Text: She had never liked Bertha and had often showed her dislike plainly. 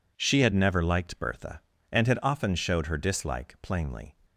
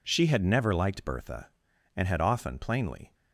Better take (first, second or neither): first